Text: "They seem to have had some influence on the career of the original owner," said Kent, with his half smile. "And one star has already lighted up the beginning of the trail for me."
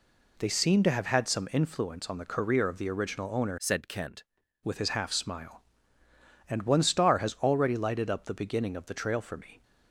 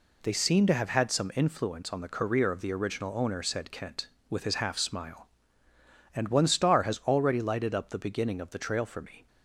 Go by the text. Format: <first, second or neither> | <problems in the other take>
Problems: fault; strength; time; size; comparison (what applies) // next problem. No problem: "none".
second | changes voice from "said" to "Kent"; from 3.5 to 4.2 s; 0.7 s long